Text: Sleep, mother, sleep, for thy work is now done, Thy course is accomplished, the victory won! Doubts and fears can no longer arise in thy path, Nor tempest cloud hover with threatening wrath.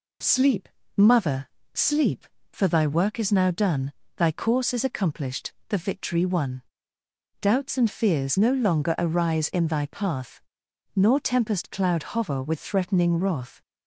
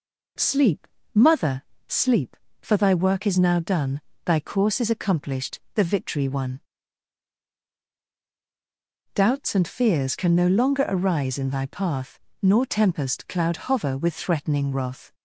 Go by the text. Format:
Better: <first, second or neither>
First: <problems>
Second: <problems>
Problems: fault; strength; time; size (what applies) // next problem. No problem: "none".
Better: second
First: skips "can"; at 8.3 s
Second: none